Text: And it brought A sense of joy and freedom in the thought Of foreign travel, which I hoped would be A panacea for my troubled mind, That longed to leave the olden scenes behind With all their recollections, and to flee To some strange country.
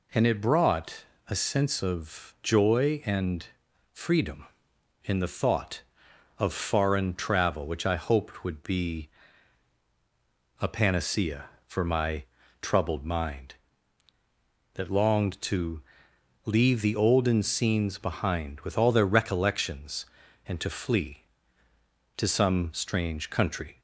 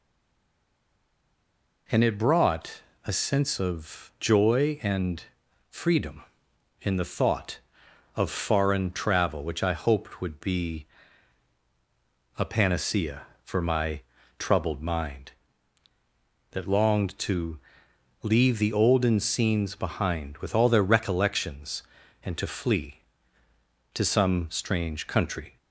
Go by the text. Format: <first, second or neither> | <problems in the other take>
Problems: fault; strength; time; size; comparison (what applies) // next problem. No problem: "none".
first | stays silent before the first word; noticeable; until 1.8 s; 1.8 s long // pauses between "brought" and "A"; slight; at 2.8 s; 0.24 s long; slight in the first // pauses between "and" and "freedom"; noticeable; at 5.2 s; 0.46 s long; noticeable in the first // pauses between "be" and "A"; strong; at 10.8 s; 1.5 s long; strong in the first // pauses between "my" and "troubled"; at 14.0 s; 0.38 s long; also in the first // pauses between "to" and "leave"; noticeable; at 17.5 s; 0.64 s long; noticeable in the first